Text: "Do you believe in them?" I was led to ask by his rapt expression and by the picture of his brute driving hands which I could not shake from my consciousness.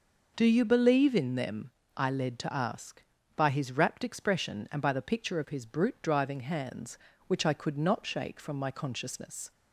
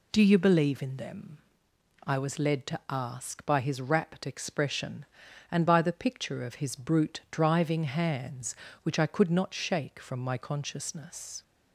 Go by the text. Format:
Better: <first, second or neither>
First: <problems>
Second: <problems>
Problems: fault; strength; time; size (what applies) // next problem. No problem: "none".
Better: second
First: skips "was"; at 2.1 s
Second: none